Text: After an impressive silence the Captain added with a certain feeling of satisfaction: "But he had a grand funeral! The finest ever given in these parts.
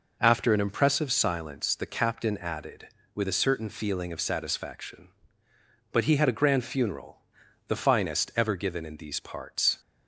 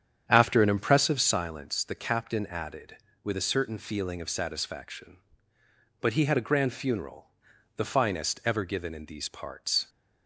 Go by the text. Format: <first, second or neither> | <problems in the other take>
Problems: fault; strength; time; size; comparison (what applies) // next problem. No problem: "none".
first | starts louder than the rest; strong; until 1.4 s; 8.5 dB